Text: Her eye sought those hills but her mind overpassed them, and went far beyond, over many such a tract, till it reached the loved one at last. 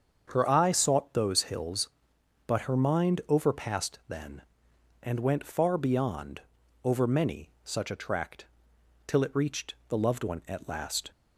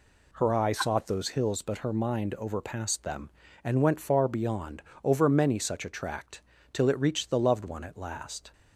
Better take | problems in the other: second | starts louder than the rest; until 1.2 s; 7 dB // says "then" for "them"; at 4.0 s

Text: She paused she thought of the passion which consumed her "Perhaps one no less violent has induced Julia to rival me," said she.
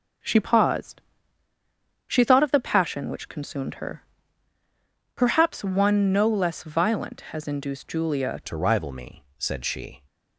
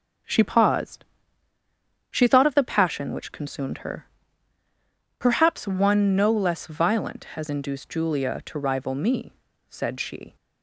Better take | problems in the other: second | pauses between "paused" and "she"; at 0.9 s; 1.0 s long; also in the second // pauses between "her" and "Perhaps"; at 4.0 s; 1.1 s long; also in the second // changes voice at "to"; from 8.4 s on; 1.6 s long

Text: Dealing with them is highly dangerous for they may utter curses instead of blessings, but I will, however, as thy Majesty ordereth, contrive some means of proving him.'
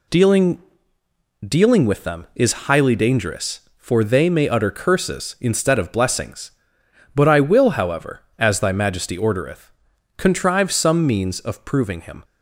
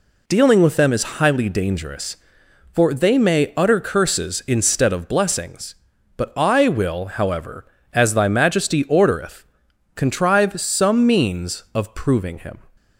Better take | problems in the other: second | says "Dealing" twice; at 1.4 s

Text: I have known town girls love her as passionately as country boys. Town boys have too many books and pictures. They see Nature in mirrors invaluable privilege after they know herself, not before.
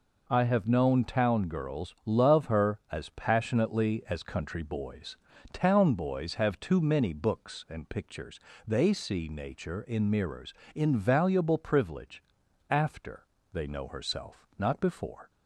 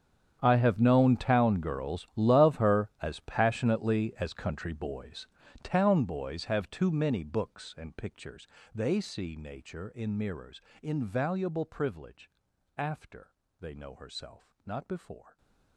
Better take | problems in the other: first | gets quieter; strong; throughout; 20 dB // pauses between "mirrors" and "invaluable"; slight; at 10.6 s; 0.22 s long; slight in the first // pauses between "privilege" and "after"; noticeable; at 12.2 s; 0.48 s long; noticeable in the first // pauses between "after" and "they"; slight; at 13.3 s; 0.30 s long; slight in the first

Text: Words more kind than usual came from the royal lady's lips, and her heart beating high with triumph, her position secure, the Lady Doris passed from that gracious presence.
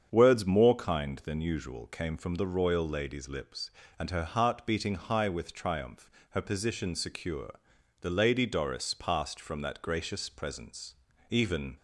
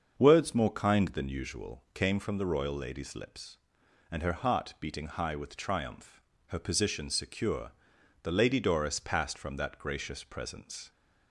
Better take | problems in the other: second | starts louder than the rest; strong; until 1.1 s; 7.5 dB; also in the second // goes on to say "Even"; slight; from 11.2 s on; 0.46 s long

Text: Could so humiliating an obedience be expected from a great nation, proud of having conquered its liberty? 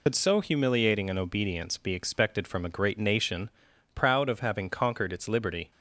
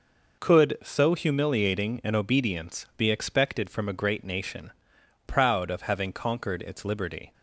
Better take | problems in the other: second | loses the start of "Could"; at 0.0 s; 70 ms

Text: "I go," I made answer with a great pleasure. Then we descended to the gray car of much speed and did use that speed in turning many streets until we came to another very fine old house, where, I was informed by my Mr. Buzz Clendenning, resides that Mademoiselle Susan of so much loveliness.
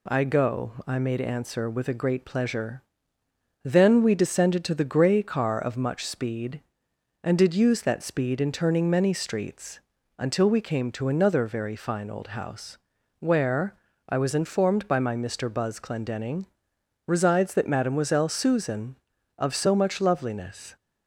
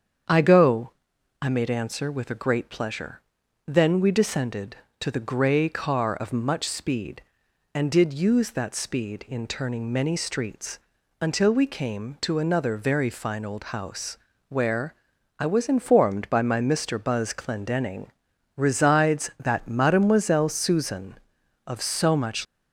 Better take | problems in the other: first | starts louder than the rest; strong; until 1.7 s; 7.5 dB // pauses between "streets" and "until"; at 10.7 s; 0.42 s long; slight in the first // stops before "loveliness"; at 22.4 s

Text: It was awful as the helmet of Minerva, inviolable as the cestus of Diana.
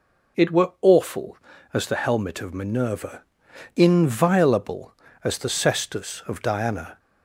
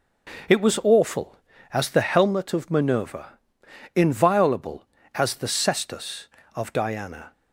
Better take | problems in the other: second | says "were" for "was"; at 0.5 s

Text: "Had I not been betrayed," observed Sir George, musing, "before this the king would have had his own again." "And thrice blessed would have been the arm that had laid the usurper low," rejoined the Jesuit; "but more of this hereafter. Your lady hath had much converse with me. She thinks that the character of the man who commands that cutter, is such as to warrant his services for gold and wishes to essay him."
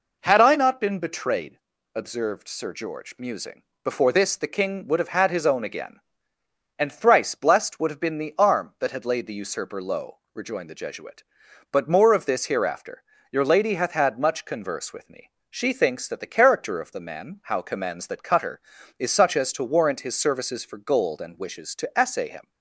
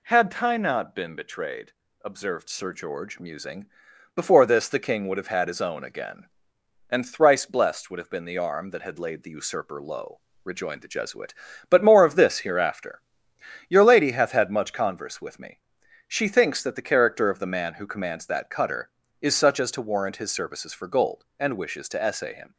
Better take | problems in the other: second | says "how" for "who"; at 17.4 s

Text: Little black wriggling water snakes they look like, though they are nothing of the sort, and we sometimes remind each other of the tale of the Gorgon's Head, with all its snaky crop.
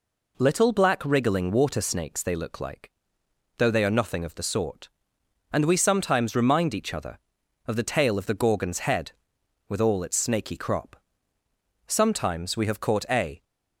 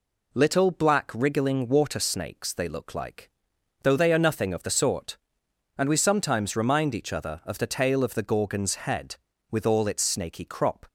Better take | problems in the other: second | goes on to say "Sometimes we have caught a"; from 11.8 s on; 1.5 s long

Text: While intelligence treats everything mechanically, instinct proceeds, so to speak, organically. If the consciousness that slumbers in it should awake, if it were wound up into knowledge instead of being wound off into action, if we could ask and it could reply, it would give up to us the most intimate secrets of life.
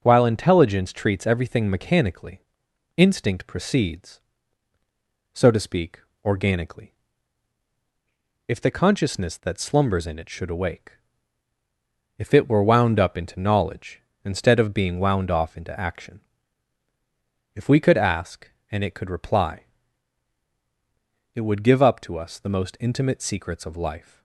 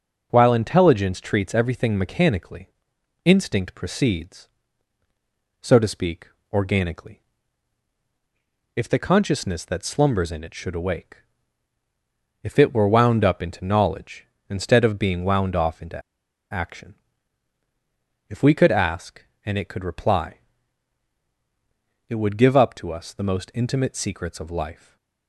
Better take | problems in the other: first | pauses between "into" and "action"; noticeable; at 16.0 s; 0.50 s long // stays silent after the last word; slight; from 24.7 s on; 0.5 s long

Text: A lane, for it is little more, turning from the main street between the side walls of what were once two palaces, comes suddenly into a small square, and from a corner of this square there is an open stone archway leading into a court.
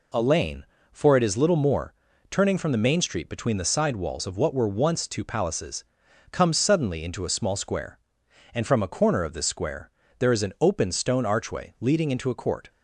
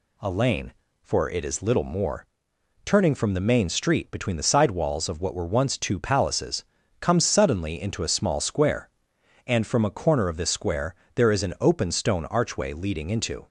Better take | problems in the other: first | pauses between "square" and "there"; slight; at 10.9 s; 0.20 s long; slight in the first // stops before "a court"; at 13.4 s

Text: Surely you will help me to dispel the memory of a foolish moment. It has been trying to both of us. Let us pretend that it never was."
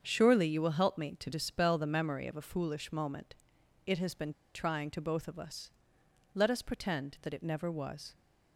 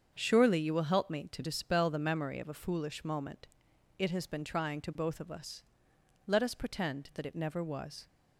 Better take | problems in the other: second | starts louder than the rest; strong; until 1.0 s; 7.5 dB; strong in the second // pauses between "been" and "trying"; slight; at 4.3 s; 0.22 s long

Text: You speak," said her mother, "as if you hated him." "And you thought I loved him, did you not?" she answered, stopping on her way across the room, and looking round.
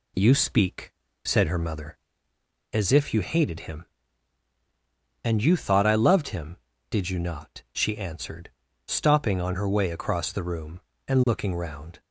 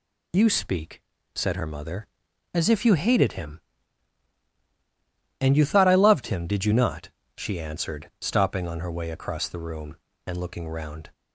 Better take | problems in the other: neither | none

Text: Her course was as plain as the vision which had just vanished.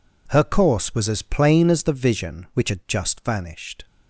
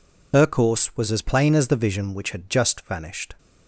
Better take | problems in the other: first | loses the start of "Her"; at 0.3 s; 85 ms

